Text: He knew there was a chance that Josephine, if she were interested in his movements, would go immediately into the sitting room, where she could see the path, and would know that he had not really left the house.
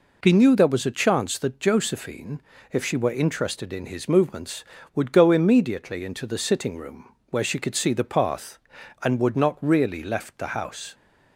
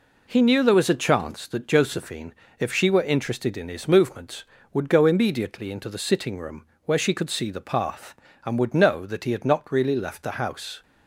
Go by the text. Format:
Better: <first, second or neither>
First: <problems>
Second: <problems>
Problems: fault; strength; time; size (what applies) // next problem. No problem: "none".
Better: second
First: skips "know that he had"; at 9.3 s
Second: none